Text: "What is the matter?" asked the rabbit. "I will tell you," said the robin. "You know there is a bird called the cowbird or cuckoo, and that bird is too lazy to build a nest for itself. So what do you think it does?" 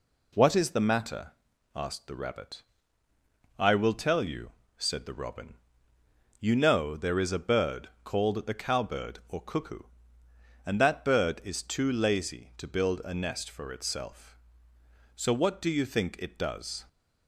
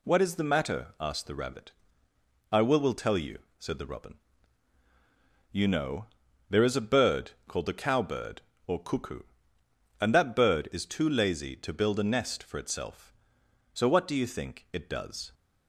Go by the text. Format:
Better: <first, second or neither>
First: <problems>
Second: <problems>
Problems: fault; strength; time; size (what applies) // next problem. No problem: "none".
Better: first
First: none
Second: says "will" twice; at 2.7 s // pauses between "know" and "there"; at 6.0 s; 0.42 s long